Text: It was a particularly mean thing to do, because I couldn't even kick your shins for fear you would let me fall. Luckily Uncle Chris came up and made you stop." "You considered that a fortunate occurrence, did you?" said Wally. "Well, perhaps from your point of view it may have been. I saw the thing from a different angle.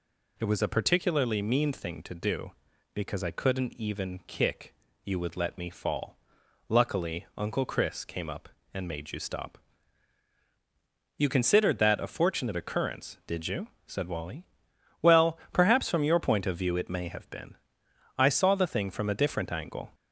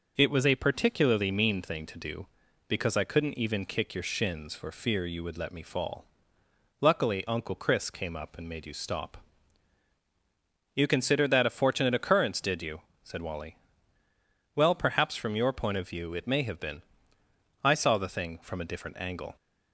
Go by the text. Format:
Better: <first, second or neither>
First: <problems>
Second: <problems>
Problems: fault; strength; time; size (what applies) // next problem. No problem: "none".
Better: second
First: skips "your shins for fear"; at 4.8 s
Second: none